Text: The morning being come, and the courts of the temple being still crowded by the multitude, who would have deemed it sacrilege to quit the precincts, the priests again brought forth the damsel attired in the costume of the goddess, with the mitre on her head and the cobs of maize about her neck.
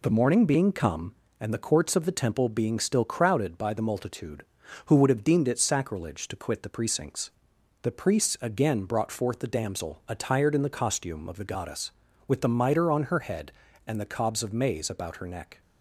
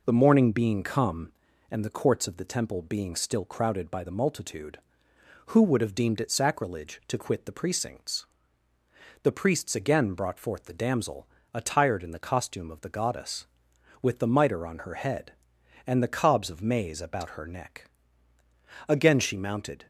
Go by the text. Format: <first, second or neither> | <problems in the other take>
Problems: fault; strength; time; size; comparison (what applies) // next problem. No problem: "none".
first | pauses between "damsel" and "attired"; slight; at 11.2 s; 0.28 s long // goes on to say "Again she mounted"; noticeable; from 18.8 s on; 1.0 s long